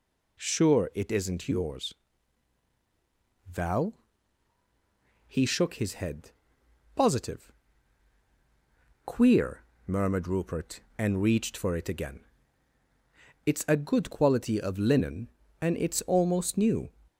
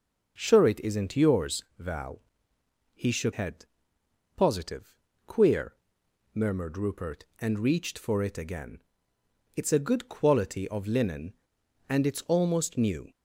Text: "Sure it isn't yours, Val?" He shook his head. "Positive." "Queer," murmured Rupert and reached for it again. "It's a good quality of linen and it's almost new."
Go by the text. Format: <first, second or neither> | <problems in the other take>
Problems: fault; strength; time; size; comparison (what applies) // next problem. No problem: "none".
first | skips "his"; at 3.3 s